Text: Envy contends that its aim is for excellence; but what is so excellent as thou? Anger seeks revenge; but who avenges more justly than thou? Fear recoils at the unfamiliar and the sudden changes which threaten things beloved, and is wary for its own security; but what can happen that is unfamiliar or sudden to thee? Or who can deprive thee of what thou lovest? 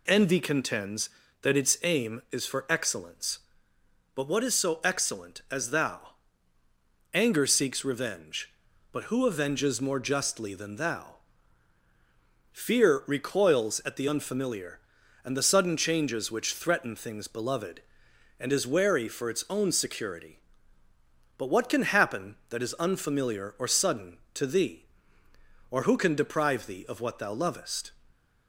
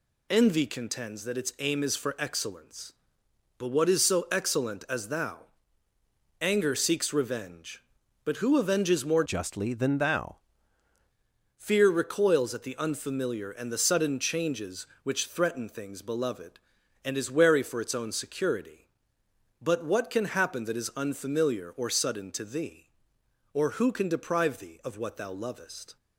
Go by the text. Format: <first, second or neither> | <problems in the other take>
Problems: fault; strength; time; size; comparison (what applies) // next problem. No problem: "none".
first | changes voice from "justly" to "thou"; from 9.2 to 10.3 s; 1.1 s long